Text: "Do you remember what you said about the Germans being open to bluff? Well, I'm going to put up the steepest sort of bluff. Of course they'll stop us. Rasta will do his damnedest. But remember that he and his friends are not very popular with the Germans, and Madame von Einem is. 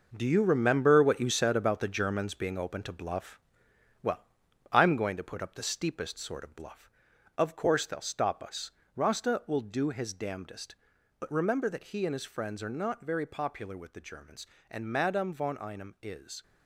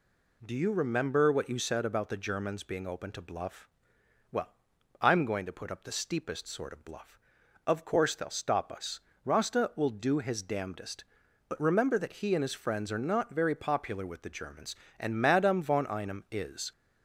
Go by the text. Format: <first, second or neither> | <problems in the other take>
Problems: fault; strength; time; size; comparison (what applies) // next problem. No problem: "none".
second | gets quieter; strong; throughout; 9 dB